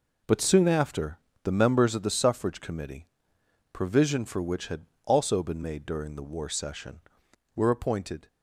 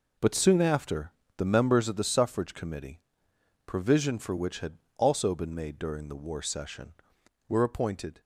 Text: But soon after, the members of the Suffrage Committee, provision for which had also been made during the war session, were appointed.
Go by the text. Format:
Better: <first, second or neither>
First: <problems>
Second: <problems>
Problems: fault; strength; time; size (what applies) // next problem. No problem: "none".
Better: neither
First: pauses between "had" and "also"; slight; at 4.8 s; 0.18 s long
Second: pauses between "had" and "also"; slight; at 4.7 s; 0.18 s long